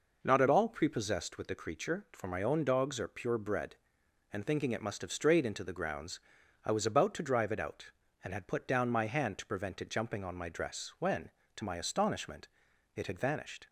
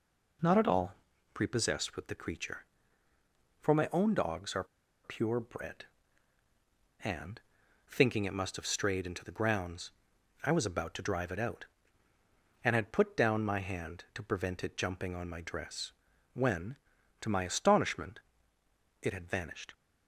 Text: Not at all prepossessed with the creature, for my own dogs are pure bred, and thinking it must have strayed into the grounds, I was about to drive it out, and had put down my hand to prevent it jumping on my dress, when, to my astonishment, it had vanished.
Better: first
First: none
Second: pauses between "all" and "prepossessed"; at 0.9 s; 0.40 s long // pauses between "are" and "pure"; at 4.6 s; 0.39 s long // pauses between "and" and "thinking"; noticeable; at 7.4 s; 0.48 s long

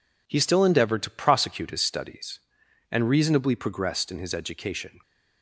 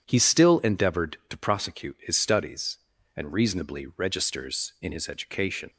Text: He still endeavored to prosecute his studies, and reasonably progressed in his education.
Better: first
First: none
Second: says "registers" for "progressed"; at 3.9 s

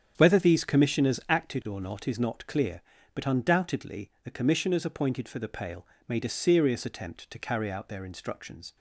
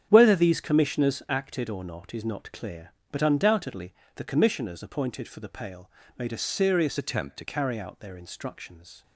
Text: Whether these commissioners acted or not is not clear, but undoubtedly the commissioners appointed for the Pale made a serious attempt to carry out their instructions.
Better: first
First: starts louder than the rest; strong; until 1.1 s; 8.5 dB // pauses between "Pale" and "made"; slight; at 5.8 s; 0.22 s long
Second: starts louder than the rest; strong; until 1.1 s; 8.5 dB // pauses between "undoubtedly" and "the"; slight; at 3.9 s; 0.22 s long // pauses between "Pale" and "made"; slight; at 5.8 s; 0.30 s long // changes voice from "attempt" to "to"; from 6.9 to 7.4 s; 0.5 s long

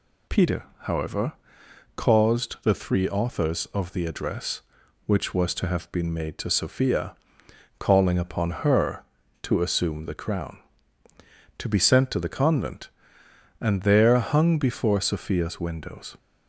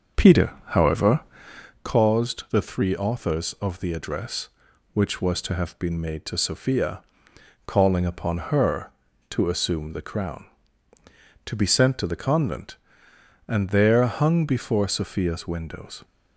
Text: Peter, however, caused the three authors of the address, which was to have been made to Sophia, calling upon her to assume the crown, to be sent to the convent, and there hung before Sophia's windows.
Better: first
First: none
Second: starts louder than the rest; until 1.8 s; 6.5 dB

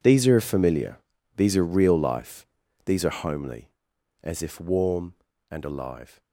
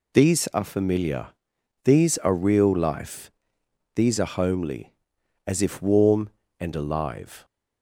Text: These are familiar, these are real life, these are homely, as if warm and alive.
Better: second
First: gets quieter; strong; throughout; 17 dB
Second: none

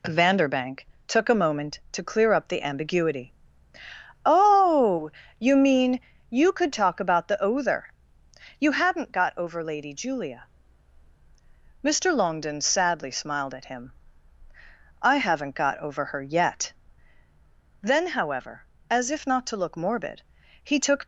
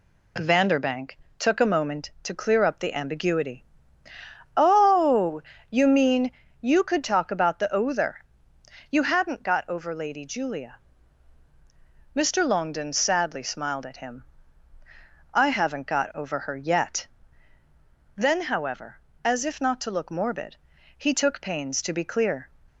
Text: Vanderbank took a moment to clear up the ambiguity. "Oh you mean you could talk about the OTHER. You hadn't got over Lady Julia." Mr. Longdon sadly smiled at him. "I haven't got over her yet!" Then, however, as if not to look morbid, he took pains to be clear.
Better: second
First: pauses between "Vanderbank" and "took"; slight; at 0.8 s; 0.22 s long // pauses between "Oh" and "you"; slight; at 5.0 s; 0.30 s long // pauses between "mean" and "you"; slight; at 5.9 s; 0.30 s long // stops before "pains to be clear"; at 21.0 s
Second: pauses between "Vanderbank" and "took"; slight; at 1.1 s; 0.22 s long // pauses between "Oh" and "you"; slight; at 5.4 s; 0.30 s long // pauses between "mean" and "you"; slight; at 6.3 s; 0.30 s long

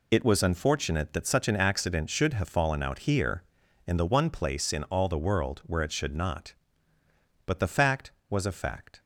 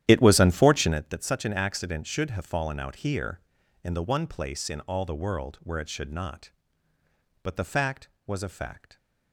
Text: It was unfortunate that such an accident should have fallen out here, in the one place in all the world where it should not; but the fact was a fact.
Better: first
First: none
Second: starts louder than the rest; strong; until 1.0 s; 11.5 dB

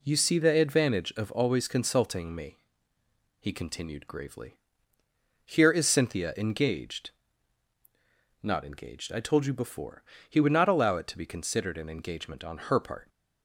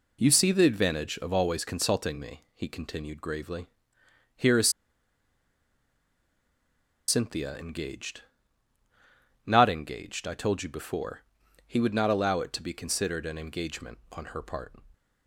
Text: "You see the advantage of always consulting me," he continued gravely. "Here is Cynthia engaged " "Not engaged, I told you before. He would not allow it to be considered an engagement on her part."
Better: first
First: none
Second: pauses between "is" and "Cynthia"; strong; at 4.6 s; 2.3 s long

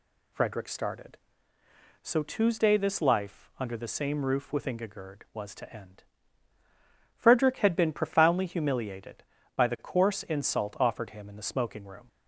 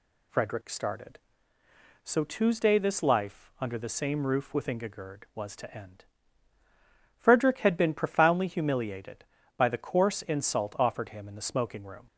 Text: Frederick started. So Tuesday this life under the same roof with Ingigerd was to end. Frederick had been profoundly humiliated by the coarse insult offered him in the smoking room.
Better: neither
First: none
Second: none

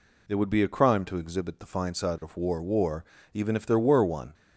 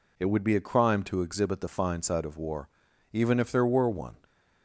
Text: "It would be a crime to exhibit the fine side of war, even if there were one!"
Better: second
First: says "war" twice; at 2.5 s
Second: none

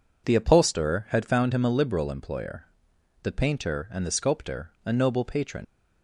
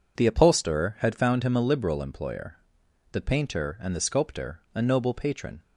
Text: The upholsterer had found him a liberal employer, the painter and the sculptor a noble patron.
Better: second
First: leaves "patron" unfinished; at 5.6 s; 75 ms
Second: none

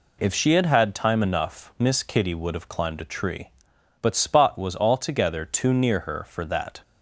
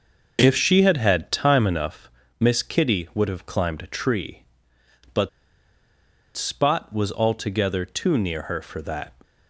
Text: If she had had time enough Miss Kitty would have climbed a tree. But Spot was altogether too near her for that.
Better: first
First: none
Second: starts louder than the rest; noticeable; until 1.4 s; 6 dB // pauses between "enough" and "Miss"; slight; at 2.0 s; 0.30 s long // pauses between "But" and "Spot"; at 5.2 s; 1.0 s long

